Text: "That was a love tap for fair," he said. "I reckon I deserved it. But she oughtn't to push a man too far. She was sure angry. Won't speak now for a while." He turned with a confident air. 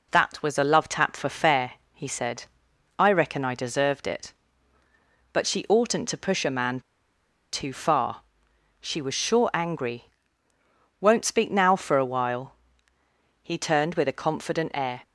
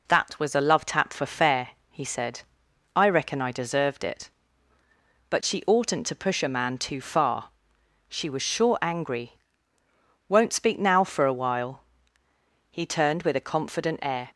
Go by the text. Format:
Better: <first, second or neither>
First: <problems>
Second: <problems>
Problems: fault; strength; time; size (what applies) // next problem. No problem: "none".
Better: second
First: pauses between "man" and "too"; noticeable; at 6.8 s; 0.72 s long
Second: none